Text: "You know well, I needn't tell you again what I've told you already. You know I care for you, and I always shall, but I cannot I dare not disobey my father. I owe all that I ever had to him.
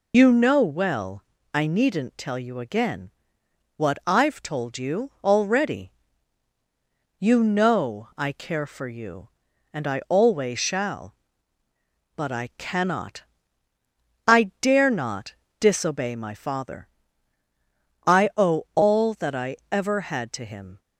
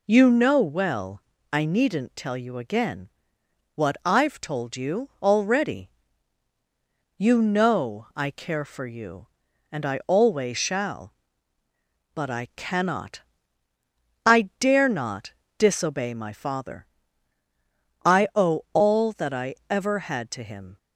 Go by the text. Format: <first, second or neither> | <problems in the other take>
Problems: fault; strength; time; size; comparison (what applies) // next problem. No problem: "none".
second | loses the start of "You"; at 0.1 s; 75 ms // pauses between "again" and "what"; noticeable; at 3.0 s; 0.68 s long; noticeable in the second // pauses between "cannot" and "I"; at 13.2 s; 1.0 s long; also in the second // pauses between "not" and "disobey"; slight; at 15.3 s; 0.26 s long; slight in the second